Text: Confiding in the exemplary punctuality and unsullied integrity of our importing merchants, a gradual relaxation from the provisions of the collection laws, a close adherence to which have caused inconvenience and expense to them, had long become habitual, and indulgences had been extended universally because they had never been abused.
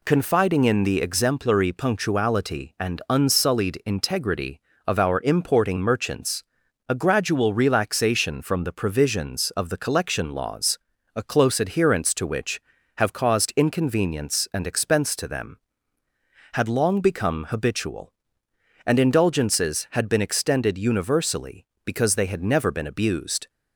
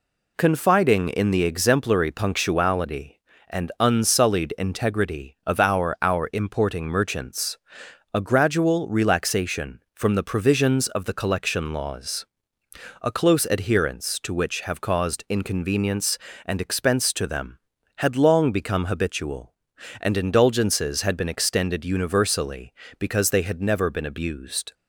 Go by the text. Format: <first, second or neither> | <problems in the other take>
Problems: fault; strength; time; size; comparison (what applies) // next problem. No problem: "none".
first | says "our" twice; at 6.0 s